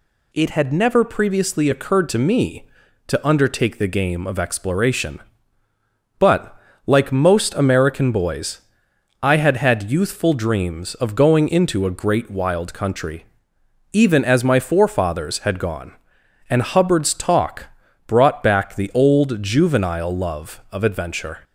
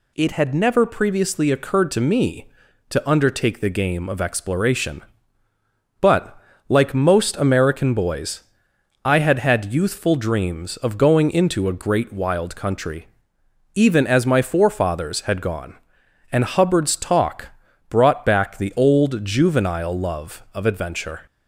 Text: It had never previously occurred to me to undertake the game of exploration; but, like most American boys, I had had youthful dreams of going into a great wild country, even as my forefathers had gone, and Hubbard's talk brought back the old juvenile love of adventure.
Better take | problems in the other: neither | pauses between "talk" and "brought"; the same in both

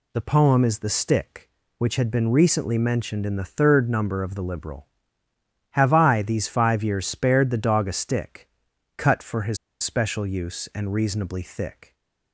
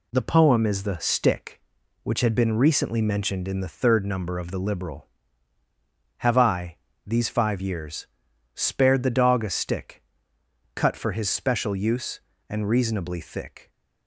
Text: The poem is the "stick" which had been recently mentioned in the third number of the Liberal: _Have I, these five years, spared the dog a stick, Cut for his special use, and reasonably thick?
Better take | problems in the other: second | pauses between "his" and "special"; slight; at 9.5 s; 0.26 s long

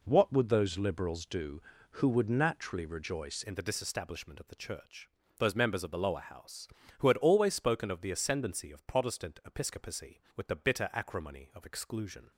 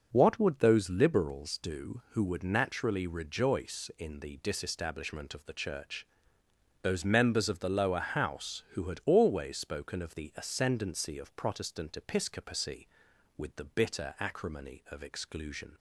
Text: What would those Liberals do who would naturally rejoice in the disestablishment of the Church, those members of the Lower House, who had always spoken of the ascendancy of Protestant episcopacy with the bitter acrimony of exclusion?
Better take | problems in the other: second | changes voice at "in"; from 3.4 s on; 8.9 s long

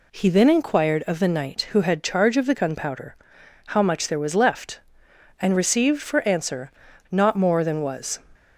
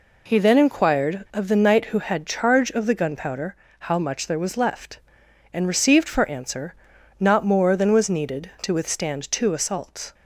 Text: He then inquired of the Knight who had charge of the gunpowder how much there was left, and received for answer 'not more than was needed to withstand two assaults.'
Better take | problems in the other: second | pauses between "gunpowder" and "how"; noticeable; at 3.1 s; 0.52 s long; slight in the second // pauses between "answer" and "not"; at 6.7 s; 0.40 s long; also in the second // stops before "needed to withstand two assaults"; at 8.3 s

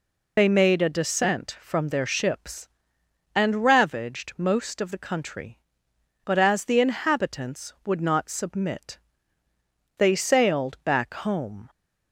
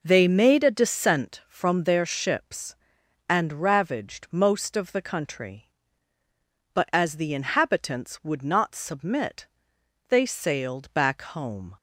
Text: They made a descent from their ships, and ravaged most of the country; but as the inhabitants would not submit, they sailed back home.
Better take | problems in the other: second | loses the start of "They"; at 0.3 s; 35 ms

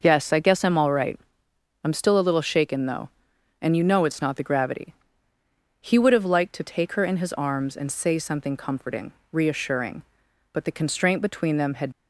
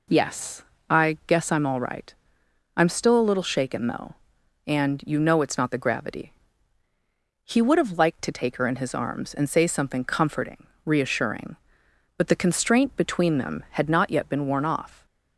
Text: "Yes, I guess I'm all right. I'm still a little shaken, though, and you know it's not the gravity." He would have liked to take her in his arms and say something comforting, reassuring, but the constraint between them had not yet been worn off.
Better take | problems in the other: second | stops before "not yet been worn off"; at 11.9 s

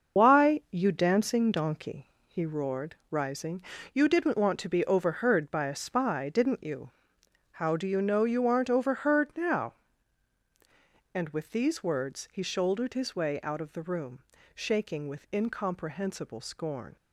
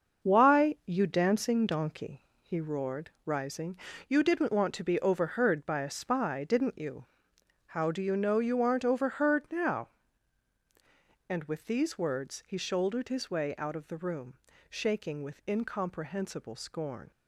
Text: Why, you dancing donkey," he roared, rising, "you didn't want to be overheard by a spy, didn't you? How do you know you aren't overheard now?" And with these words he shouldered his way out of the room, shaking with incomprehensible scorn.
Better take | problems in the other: second | loses the start of "Why"; at 0.1 s; 80 ms // starts louder than the rest; until 1.2 s; 6.5 dB; also in the second

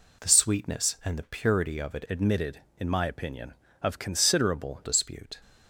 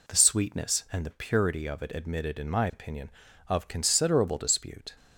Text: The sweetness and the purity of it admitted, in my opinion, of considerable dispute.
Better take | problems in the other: second | changes voice from "admitted" to "considerable"; from 2.0 to 4.8 s; 2.8 s long

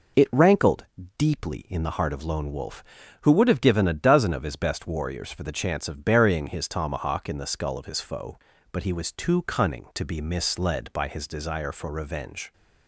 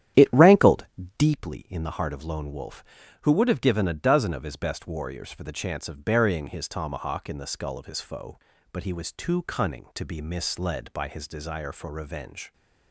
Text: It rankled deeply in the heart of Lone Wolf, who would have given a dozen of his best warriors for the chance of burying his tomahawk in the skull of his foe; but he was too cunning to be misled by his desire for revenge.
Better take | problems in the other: first | starts louder than the rest; strong; until 1.3 s; 11 dB // pauses between "rankled" and "deeply"; slight; at 0.8 s; 0.34 s long; slight in the first

